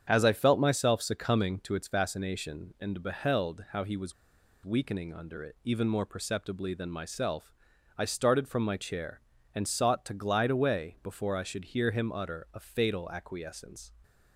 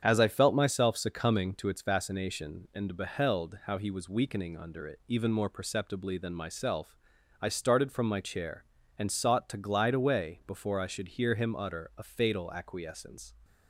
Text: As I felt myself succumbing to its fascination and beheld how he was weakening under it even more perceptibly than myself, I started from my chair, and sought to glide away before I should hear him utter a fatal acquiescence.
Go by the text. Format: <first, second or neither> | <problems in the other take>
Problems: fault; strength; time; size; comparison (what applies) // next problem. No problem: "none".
second | starts louder than the rest; strong; until 1.0 s; 8 dB; strong in the second // pauses between "was" and "weakening"; noticeable; at 4.1 s; 0.52 s long